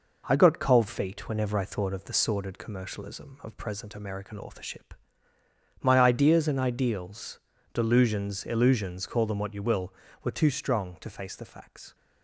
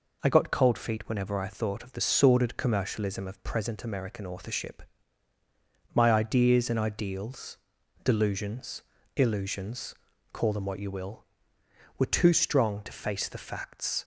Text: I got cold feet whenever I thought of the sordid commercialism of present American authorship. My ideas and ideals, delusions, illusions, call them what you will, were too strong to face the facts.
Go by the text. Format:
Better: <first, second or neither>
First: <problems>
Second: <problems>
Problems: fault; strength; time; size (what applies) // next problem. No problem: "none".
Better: second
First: gets quieter; slight; throughout; 3 dB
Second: none